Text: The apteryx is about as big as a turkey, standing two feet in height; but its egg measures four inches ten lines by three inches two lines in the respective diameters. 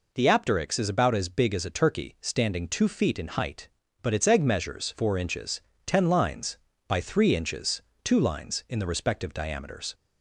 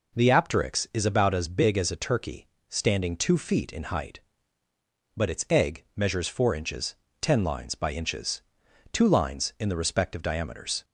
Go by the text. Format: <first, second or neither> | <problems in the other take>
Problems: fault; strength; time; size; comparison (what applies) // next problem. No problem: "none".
first | pauses between "inches" and "ten"; slight; at 6.9 s; 0.26 s long; slight in the first // skips "three"; at 7.9 s // pauses between "inches" and "two"; noticeable; at 8.3 s; 0.52 s long; slight in the first